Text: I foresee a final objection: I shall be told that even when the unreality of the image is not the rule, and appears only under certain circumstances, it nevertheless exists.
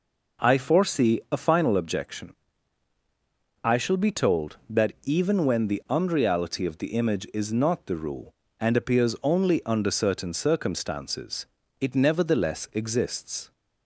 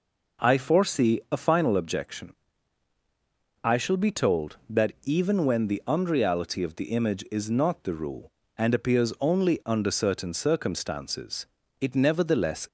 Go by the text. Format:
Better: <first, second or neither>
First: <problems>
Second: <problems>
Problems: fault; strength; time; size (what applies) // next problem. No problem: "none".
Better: first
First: none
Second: stops before "exists"; at 12.6 s